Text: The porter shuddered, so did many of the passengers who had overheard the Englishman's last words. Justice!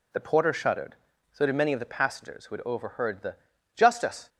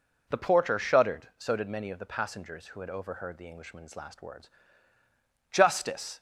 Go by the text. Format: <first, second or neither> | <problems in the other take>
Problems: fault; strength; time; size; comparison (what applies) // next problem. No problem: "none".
second | skips "Englishman's last words"; at 3.5 s